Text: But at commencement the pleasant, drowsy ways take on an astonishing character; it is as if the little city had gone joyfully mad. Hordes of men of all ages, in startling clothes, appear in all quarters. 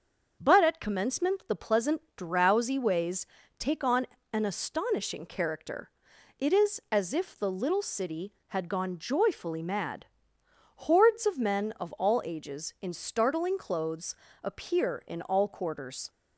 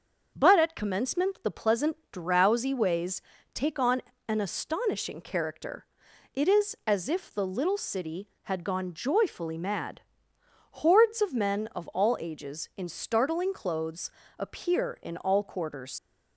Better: first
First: starts louder than the rest; until 1.3 s; 6.5 dB // pauses between "ways" and "take"; slight; at 3.2 s; 0.34 s long // pauses between "on" and "an"; slight; at 4.0 s; 0.26 s long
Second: starts louder than the rest; until 1.3 s; 6.5 dB // pauses between "ways" and "take"; slight; at 3.2 s; 0.34 s long // pauses between "on" and "an"; slight; at 4.0 s; 0.26 s long // leaves "quarters" unfinished; at 15.9 s; 60 ms

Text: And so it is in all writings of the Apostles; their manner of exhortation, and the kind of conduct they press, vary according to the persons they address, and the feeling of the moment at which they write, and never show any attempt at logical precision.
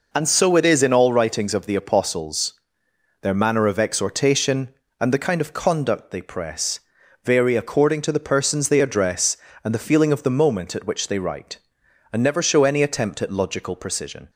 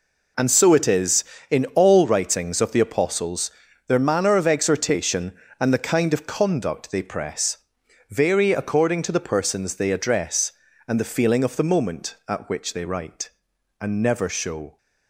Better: first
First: none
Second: stops before "any attempt at logical precision"; at 14.7 s

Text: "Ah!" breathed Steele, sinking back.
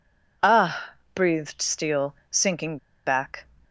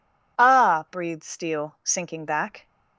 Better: second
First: pauses between "sinking" and "back"; slight; at 2.7 s; 0.28 s long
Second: none

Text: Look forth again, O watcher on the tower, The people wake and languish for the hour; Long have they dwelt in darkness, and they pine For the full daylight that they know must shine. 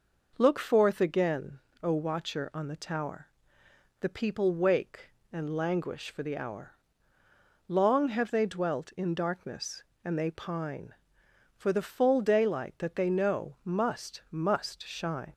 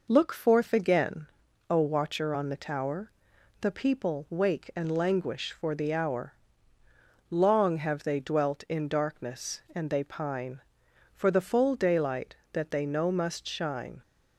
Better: second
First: says "must" twice; at 14.3 s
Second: none

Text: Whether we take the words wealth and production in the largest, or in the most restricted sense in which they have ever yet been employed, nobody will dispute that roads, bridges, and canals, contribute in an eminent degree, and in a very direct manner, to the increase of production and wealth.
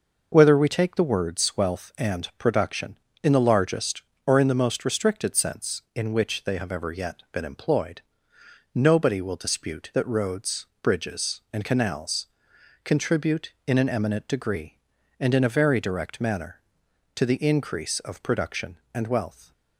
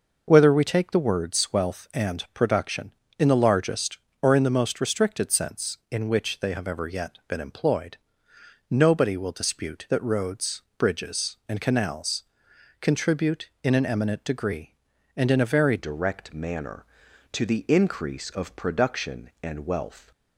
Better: first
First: none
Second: changes voice at "direct"; from 15.7 s on; 4.4 s long

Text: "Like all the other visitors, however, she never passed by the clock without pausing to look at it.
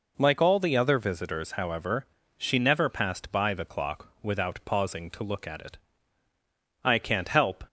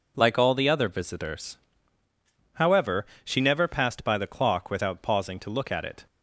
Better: second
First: goes on to say "I can't help"; noticeable; from 6.8 s on; 0.80 s long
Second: none

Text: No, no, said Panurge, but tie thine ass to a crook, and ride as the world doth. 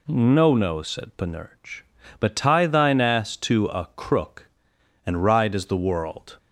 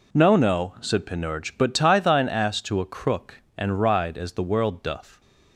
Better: second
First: stops before "doth"; at 6.3 s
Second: none

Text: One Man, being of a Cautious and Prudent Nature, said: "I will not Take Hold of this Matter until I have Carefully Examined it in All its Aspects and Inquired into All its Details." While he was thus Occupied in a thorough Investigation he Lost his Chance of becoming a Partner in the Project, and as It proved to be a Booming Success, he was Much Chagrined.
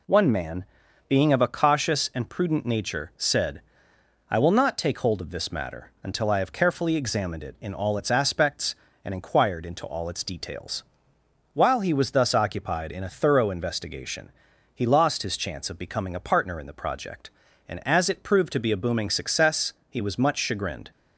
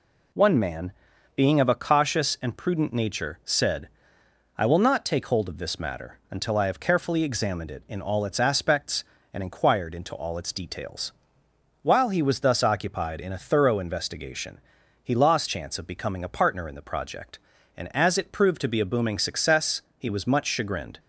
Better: first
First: pauses between "Investigation" and "he"; at 14.3 s; 0.44 s long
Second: pauses between "Investigation" and "he"; at 14.5 s; 0.44 s long // skips "his"; at 15.4 s

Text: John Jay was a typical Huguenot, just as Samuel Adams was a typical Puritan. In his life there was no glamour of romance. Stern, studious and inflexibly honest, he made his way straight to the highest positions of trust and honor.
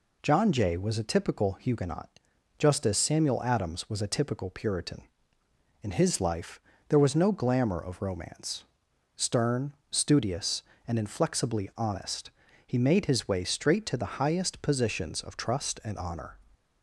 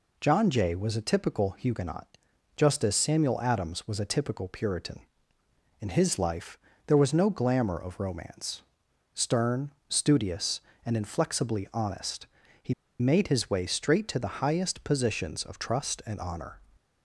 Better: first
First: pauses between "life" and "there"; slight; at 6.5 s; 0.30 s long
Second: pauses between "life" and "there"; slight; at 6.5 s; 0.30 s long // pauses between "he" and "made"; slight; at 12.7 s; 0.26 s long

